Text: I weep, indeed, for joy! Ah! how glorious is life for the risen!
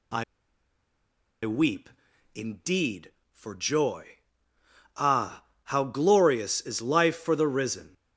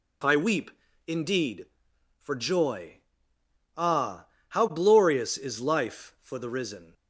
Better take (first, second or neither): second